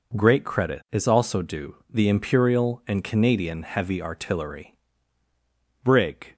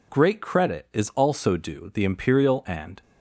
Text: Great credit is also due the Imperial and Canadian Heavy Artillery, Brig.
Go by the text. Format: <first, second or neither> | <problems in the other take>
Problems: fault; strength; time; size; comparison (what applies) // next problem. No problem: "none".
first | stops before "Canadian Heavy Artillery Brig"; at 3.0 s